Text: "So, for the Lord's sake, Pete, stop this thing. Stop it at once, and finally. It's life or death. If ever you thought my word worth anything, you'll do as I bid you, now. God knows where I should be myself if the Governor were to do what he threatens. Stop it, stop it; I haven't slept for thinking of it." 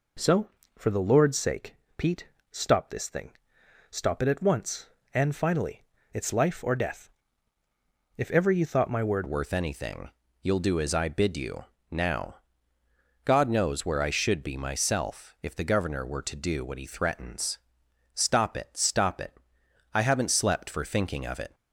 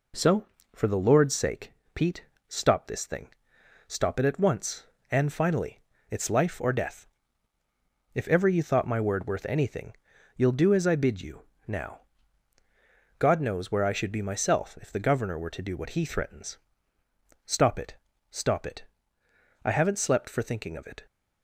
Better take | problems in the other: second | changes voice at "worth"; from 9.2 s on; 12.3 s long

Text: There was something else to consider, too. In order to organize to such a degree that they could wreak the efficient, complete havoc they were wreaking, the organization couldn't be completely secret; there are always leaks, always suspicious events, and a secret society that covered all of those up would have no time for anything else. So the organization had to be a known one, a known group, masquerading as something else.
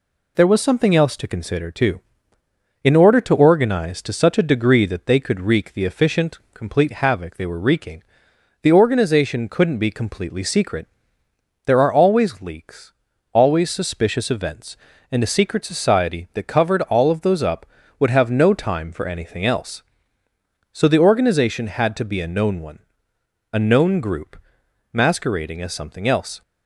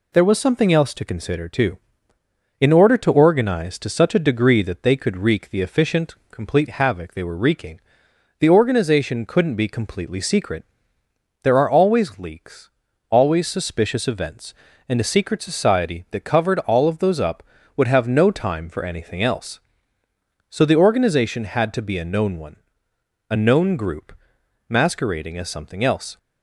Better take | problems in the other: neither | none

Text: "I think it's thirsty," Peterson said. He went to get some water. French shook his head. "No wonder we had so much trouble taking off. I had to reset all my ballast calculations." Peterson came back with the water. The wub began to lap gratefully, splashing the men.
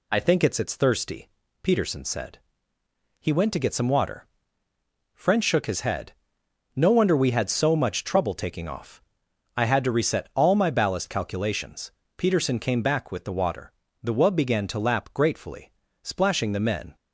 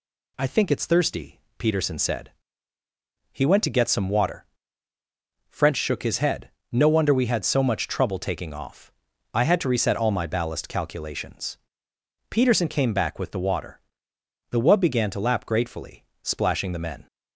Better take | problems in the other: second | says "it's" twice; at 0.5 s

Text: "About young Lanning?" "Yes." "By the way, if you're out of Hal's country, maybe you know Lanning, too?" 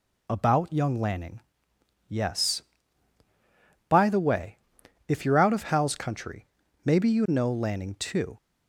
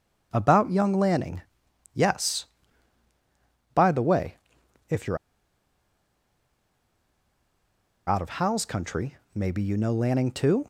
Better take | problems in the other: first | pauses between "you're" and "out"; strong; at 5.1 s; 2.9 s long

